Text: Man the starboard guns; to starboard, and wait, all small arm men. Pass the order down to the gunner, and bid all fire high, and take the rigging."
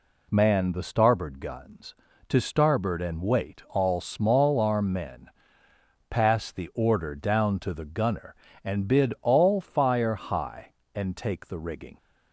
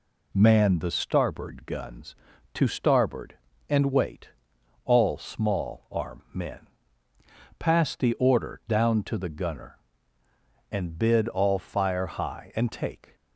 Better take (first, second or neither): first